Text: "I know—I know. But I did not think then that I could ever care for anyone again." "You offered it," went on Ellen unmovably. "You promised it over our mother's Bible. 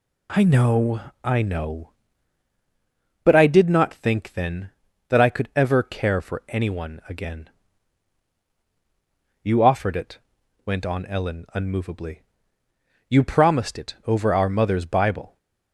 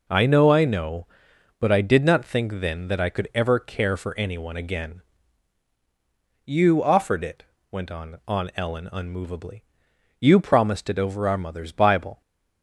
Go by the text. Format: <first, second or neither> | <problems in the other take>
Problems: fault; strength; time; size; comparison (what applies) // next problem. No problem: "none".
first | says "on" twice; at 8.2 s